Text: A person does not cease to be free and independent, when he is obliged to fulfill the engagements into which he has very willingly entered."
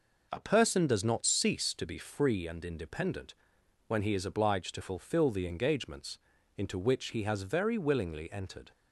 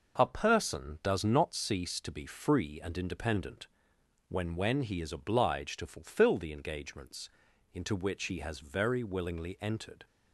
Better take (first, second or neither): first